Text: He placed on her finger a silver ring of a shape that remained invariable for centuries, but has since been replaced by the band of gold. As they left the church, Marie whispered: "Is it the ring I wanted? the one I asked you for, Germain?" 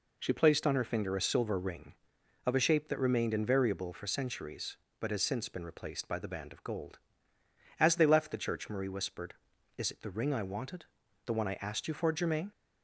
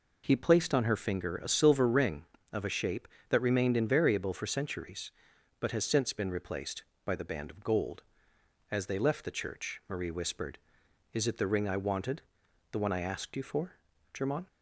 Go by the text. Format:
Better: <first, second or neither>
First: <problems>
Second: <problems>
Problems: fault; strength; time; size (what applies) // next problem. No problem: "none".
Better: second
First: says "She" for "He"; at 0.1 s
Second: none